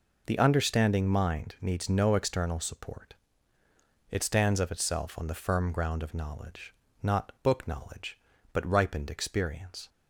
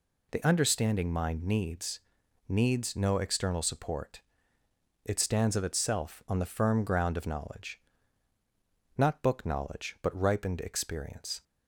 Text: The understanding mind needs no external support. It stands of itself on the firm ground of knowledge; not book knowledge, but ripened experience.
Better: first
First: none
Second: says "needs" twice; at 2.4 s

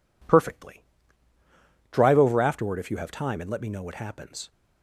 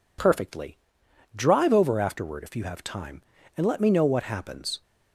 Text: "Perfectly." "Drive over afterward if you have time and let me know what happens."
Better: neither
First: none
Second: none

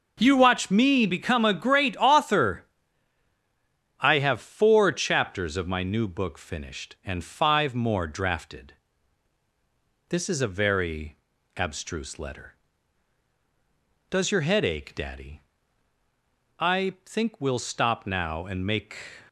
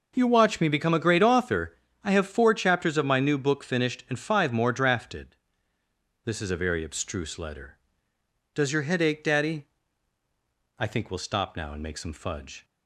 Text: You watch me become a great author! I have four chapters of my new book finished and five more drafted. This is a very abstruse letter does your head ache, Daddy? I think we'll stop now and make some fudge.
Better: second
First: pauses between "very" and "abstruse"; at 11.1 s; 0.40 s long // stops before "some fudge"; at 19.2 s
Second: none

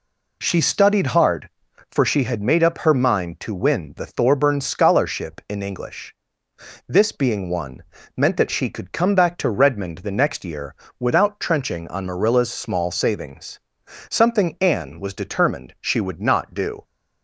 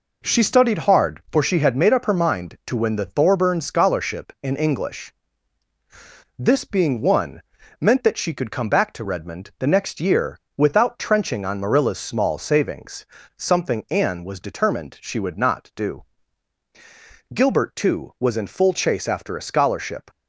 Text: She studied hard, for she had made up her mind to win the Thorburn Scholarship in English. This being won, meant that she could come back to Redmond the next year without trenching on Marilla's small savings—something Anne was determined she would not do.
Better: first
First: pauses between "year" and "without"; slight; at 10.7 s; 0.24 s long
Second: pauses between "year" and "without"; slight; at 10.3 s; 0.20 s long // goes on to say "Gilbert too was in full chase after a scholarship"; strong; from 17.3 s on; 2.7 s long

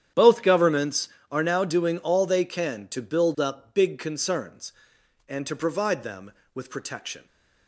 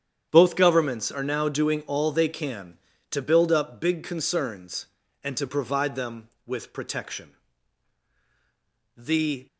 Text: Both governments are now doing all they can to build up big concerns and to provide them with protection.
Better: first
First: starts louder than the rest; strong; until 1.4 s; 10 dB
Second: starts louder than the rest; strong; until 1.3 s; 8.5 dB // goes on to say "The"; from 8.9 s on; 0.50 s long

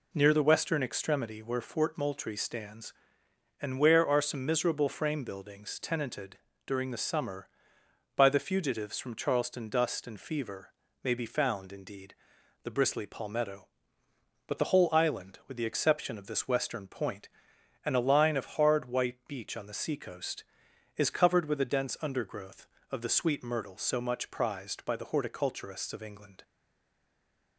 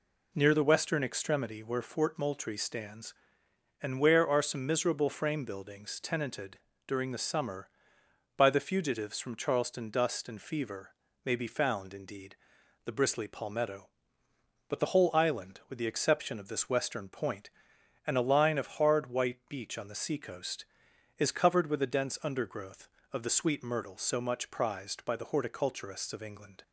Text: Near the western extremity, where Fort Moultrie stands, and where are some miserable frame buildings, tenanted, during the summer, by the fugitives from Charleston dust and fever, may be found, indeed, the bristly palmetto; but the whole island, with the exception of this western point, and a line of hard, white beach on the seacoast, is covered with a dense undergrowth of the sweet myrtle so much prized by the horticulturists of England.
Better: second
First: stays silent after the last word; from 26.4 s on; 1.1 s long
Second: none

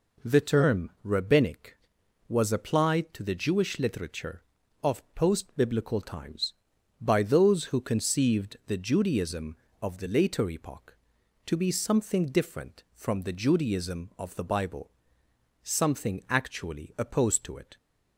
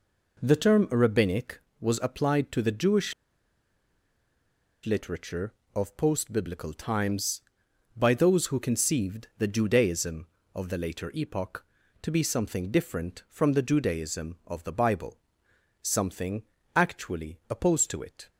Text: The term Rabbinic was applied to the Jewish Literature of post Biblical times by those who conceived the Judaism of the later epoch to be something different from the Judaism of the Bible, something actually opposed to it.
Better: first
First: none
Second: pauses between "Jewish" and "Literature"; strong; at 3.1 s; 1.7 s long // pauses between "something" and "actually"; slight; at 16.4 s; 0.30 s long

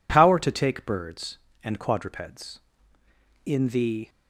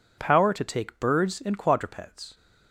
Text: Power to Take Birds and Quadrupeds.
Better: second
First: goes on to say "In the"; noticeable; from 3.4 s on; 0.64 s long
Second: none

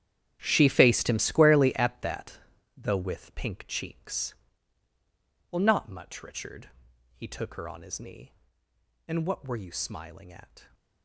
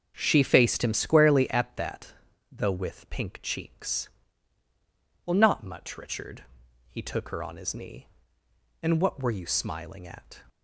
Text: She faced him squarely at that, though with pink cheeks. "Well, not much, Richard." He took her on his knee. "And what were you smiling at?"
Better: second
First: gets quieter; strong; throughout; 14.5 dB // starts louder than the rest; strong; until 1.4 s; 10.5 dB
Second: starts louder than the rest; strong; until 1.1 s; 7 dB

